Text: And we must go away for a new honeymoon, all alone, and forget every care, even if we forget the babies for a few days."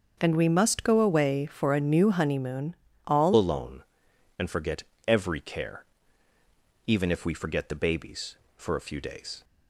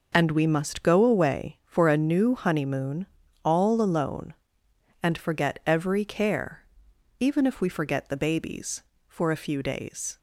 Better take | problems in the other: second | starts louder than the rest; until 1.2 s; 6.5 dB // changes voice at "alone"; from 3.3 s on; 6.1 s long // pauses between "forget" and "every"; slight; at 4.8 s; 0.22 s long

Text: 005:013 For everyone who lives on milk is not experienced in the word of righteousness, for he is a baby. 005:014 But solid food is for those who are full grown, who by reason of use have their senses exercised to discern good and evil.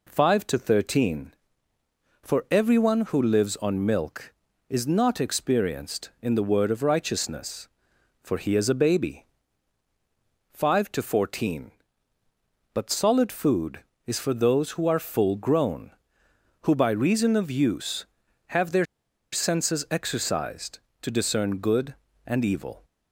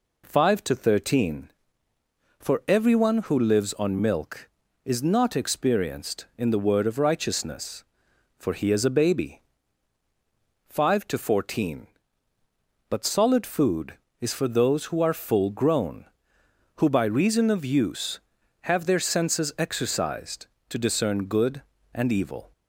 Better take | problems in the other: second | pauses between "their" and "senses"; noticeable; at 18.8 s; 0.46 s long

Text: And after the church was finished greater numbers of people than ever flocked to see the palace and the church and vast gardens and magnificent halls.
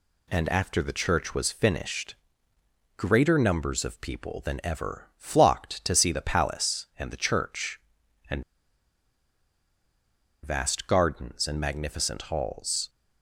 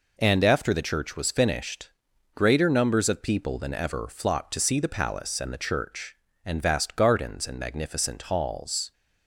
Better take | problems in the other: second | pauses between "finished" and "greater"; noticeable; at 2.1 s; 0.84 s long; noticeable in the second // pauses between "and" and "vast"; strong; at 8.4 s; 2.0 s long

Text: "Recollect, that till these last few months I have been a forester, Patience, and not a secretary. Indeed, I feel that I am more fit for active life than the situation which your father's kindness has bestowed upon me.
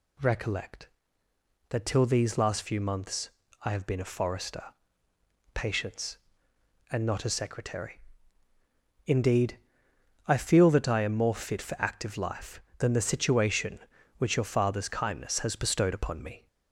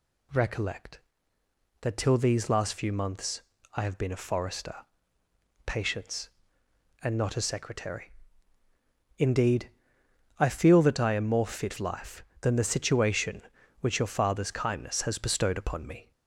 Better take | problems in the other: first | pauses between "months" and "I"; slight; at 3.4 s; 0.32 s long; slight in the first // skips "for active"; at 11.7 s

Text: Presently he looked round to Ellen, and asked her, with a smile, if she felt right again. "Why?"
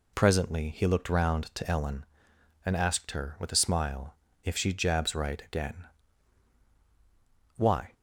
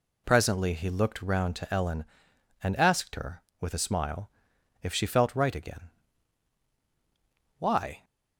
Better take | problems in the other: second | says "jabs" for "felt"; at 4.7 s

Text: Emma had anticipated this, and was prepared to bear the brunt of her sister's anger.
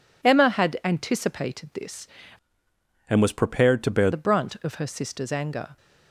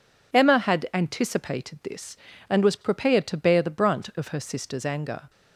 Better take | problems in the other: second | changes voice from "and" to "bear"; from 3.0 to 4.0 s; 1.0 s long

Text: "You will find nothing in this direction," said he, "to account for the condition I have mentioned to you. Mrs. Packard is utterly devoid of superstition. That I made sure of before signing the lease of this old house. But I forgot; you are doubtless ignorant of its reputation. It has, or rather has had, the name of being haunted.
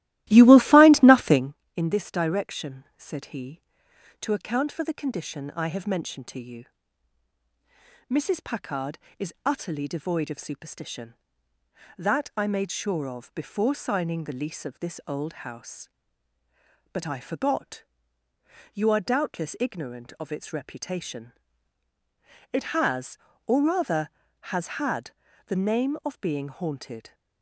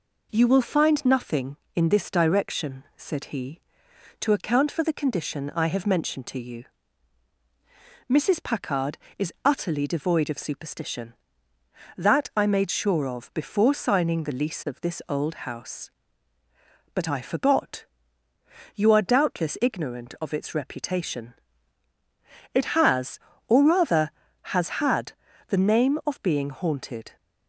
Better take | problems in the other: second | starts louder than the rest; strong; until 1.6 s; 15.5 dB

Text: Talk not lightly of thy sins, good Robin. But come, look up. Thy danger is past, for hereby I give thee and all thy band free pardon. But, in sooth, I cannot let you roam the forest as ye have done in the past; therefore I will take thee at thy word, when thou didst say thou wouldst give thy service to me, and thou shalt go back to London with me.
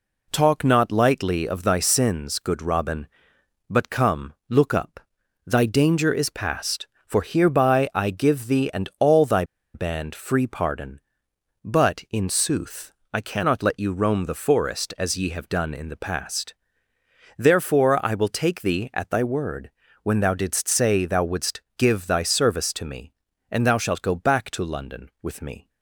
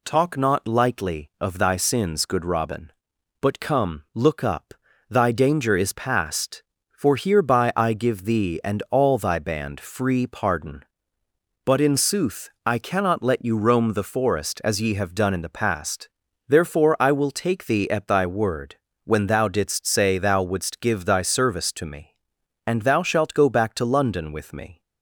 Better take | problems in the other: second | pauses between "thy" and "band"; slight; at 9.4 s; 0.30 s long // pauses between "wouldst" and "give"; slight; at 21.6 s; 0.16 s long

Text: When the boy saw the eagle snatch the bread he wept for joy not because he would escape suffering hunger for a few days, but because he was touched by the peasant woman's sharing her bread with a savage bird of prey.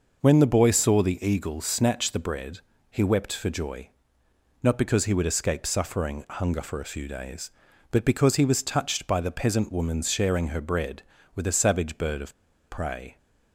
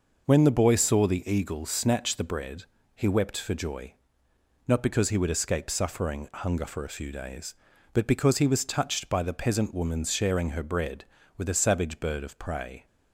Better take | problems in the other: second | pauses between "bread" and "he"; slight; at 2.5 s; 0.32 s long; slight in the second // pauses between "joy" and "not"; noticeable; at 3.8 s; 0.74 s long; noticeable in the second // pauses between "of" and "prey"; slight; at 12.3 s; 0.35 s long

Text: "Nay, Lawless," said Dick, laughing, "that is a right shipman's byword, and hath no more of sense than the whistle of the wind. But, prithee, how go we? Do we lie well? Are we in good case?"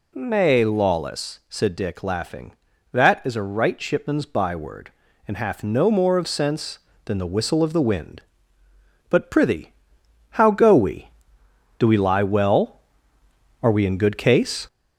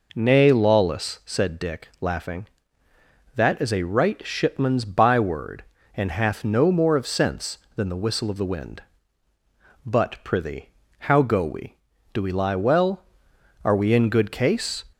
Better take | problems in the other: second | gets louder; slight; throughout; 3 dB

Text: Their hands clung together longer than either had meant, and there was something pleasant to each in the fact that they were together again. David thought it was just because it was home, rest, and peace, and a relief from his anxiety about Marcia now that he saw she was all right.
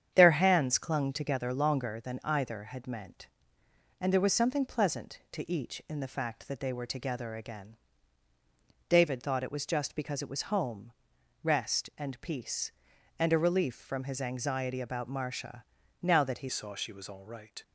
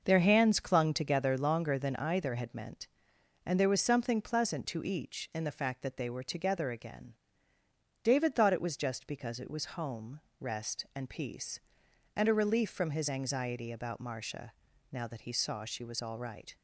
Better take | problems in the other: second | starts louder than the rest; strong; until 1.1 s; 8.5 dB // pauses between "Marcia" and "now"; at 15.6 s; 0.40 s long; also in the second // changes voice at "saw"; from 16.4 s on; 1.2 s long

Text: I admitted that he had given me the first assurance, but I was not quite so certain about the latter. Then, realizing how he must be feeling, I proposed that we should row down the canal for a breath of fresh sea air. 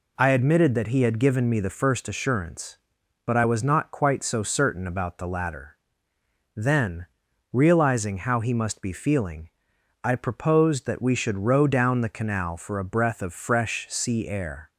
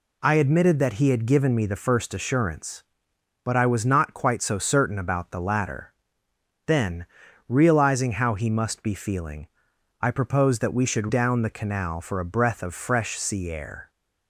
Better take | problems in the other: first | skips "row"; at 11.0 s

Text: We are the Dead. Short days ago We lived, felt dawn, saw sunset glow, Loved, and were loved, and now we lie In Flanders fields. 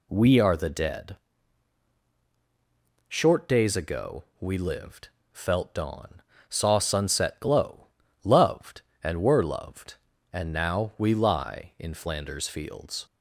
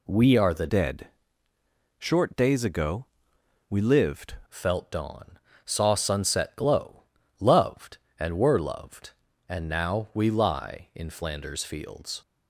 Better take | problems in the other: first | changes voice from "Dead" to "lived"; from 0.6 to 4.3 s; 3.7 s long // pauses between "ago" and "We"; noticeable; at 3.0 s; 0.64 s long; slight in the first

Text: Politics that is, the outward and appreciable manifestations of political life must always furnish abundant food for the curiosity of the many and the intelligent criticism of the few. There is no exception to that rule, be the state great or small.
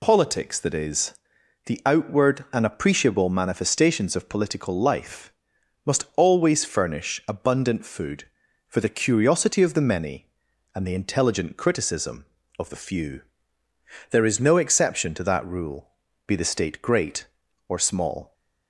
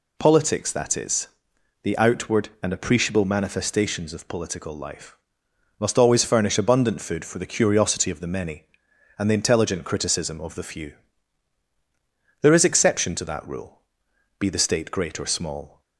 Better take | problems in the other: first | pauses between "life" and "must"; noticeable; at 5.1 s; 0.64 s long; noticeable in the first // skips "no"; at 12.6 s

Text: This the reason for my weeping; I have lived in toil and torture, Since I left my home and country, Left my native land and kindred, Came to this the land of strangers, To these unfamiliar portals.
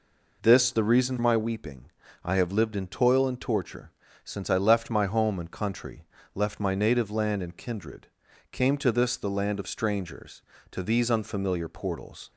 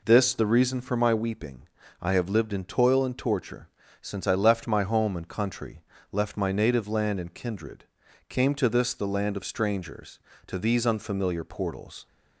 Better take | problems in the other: second | skips "for"; at 1.1 s

